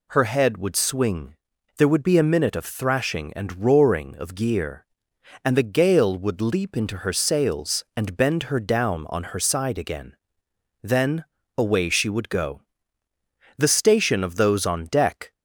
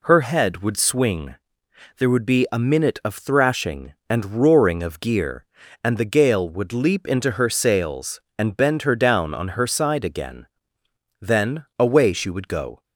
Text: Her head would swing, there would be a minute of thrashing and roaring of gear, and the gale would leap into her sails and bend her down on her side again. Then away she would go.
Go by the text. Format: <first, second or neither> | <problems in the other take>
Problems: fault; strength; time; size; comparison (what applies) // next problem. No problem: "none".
second | pauses between "Then" and "away"; slight; at 11.2 s; 0.34 s long // goes on to say "The station of those on deck"; strong; from 13.5 s on; 1.7 s long